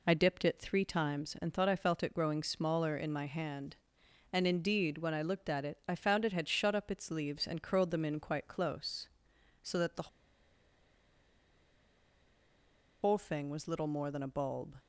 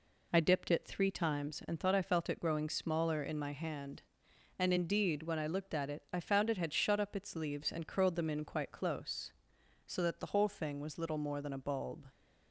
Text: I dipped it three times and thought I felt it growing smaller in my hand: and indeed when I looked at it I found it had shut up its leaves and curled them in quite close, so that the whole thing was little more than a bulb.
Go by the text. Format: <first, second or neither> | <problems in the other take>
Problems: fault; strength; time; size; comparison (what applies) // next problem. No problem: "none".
second | pauses between "the" and "whole"; strong; at 10.0 s; 2.9 s long